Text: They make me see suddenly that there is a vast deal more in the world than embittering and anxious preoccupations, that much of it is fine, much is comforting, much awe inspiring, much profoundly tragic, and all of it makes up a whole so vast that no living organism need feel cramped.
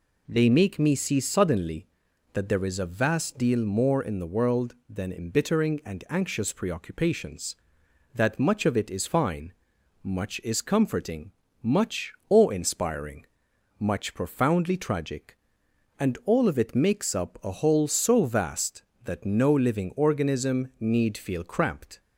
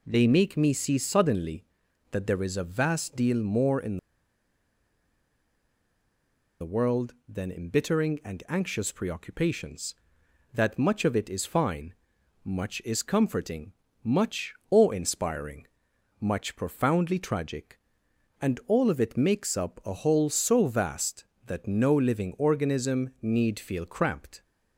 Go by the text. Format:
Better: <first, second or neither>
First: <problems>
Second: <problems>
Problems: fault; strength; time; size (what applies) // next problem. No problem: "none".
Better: first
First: pauses between "much" and "awe"; slight; at 12.1 s; 0.16 s long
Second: pauses between "in" and "the"; strong; at 3.9 s; 2.6 s long // pauses between "much" and "awe"; slight; at 14.5 s; 0.16 s long